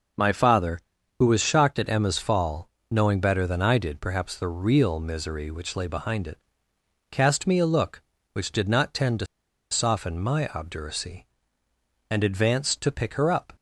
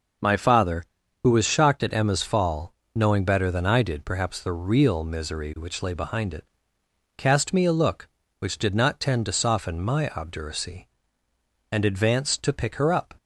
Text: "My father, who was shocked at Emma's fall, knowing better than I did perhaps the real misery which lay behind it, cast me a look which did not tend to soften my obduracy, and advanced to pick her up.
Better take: second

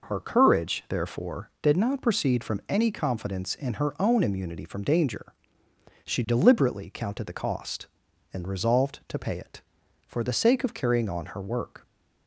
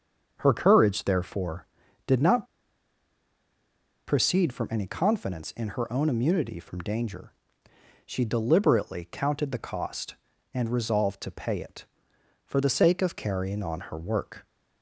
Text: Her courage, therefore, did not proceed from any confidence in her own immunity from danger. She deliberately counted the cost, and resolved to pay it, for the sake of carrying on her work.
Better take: first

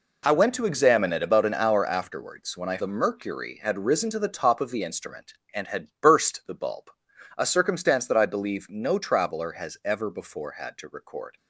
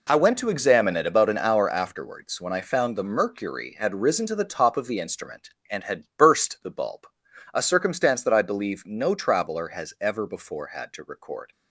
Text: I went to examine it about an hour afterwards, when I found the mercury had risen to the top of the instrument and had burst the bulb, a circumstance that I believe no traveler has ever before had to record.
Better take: second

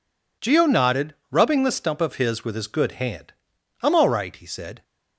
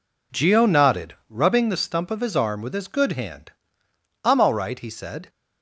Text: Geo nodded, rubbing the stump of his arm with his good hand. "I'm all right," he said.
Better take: second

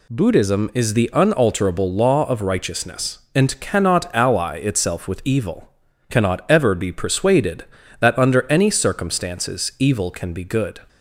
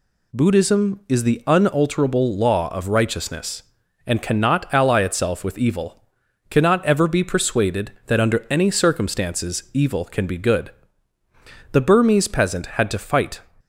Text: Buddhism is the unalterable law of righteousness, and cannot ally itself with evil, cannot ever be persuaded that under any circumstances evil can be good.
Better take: first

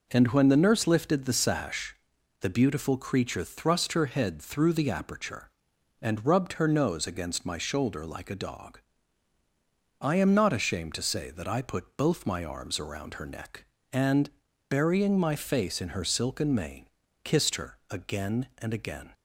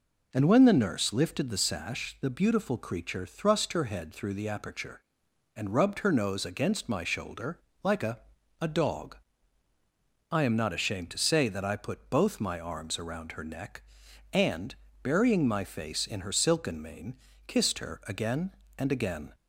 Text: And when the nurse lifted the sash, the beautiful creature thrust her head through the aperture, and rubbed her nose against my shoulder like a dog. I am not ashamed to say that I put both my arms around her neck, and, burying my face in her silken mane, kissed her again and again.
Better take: first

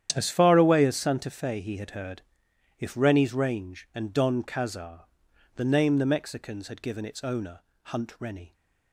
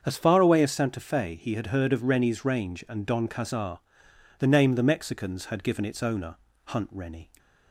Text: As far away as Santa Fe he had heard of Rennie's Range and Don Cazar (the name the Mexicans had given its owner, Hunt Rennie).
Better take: second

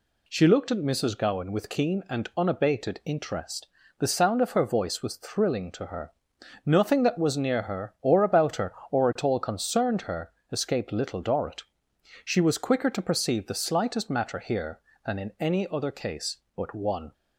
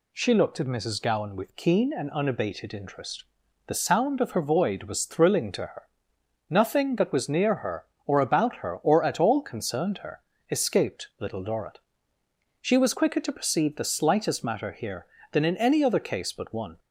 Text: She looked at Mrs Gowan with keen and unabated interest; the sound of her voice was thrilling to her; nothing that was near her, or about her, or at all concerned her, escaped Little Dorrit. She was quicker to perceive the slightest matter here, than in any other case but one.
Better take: first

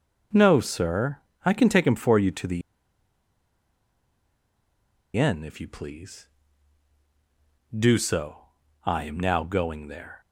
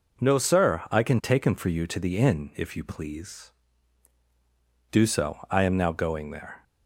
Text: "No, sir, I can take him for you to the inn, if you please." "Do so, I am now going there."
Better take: second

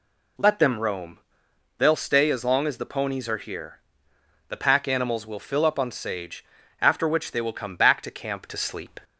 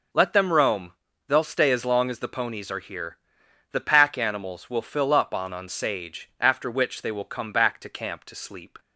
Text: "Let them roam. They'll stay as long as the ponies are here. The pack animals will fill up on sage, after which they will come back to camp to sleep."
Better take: first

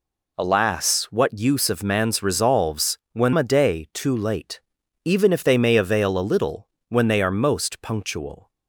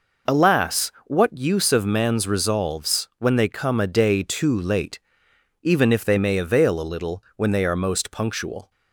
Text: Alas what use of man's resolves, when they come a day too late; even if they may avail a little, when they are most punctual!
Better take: second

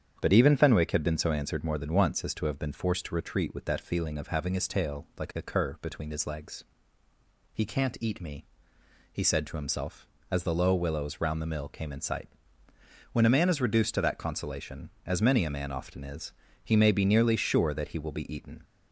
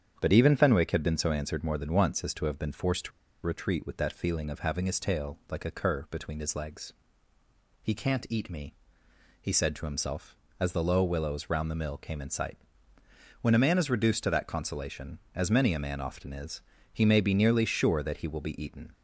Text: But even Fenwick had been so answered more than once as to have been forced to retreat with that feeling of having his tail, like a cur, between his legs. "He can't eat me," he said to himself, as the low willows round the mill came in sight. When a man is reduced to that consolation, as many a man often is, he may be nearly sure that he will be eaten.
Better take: first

